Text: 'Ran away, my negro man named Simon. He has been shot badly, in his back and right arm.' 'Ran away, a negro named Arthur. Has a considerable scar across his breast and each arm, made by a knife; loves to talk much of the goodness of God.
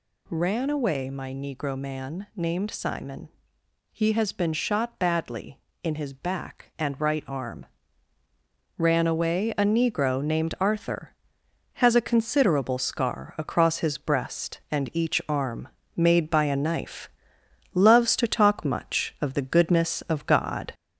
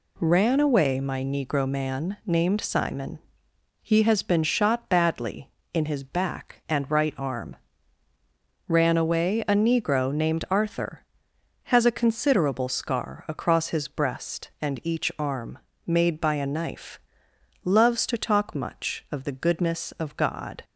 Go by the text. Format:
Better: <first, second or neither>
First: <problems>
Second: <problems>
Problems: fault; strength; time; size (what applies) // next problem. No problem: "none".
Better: second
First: gets louder; slight; throughout; 3 dB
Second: none